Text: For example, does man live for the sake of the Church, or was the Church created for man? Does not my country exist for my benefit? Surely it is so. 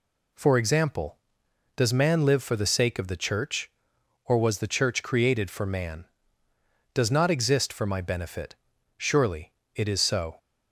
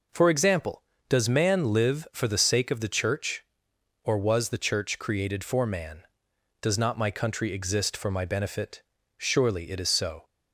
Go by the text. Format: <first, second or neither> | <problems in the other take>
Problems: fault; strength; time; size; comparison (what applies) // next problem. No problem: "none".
second | skips "my country"; at 7.2 s // pauses between "Surely" and "it"; slight; at 9.5 s; 0.24 s long